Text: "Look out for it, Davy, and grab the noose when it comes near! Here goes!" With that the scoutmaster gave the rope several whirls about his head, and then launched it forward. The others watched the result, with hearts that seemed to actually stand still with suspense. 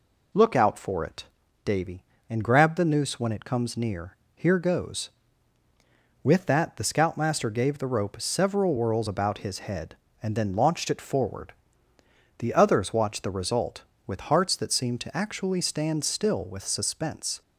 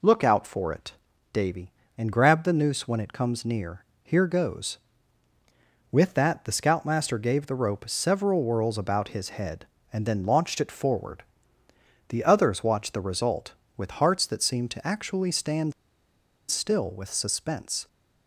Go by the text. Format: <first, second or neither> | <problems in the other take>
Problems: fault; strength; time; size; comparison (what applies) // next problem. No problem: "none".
first | pauses between "stand" and "still"; noticeable; at 15.7 s; 0.76 s long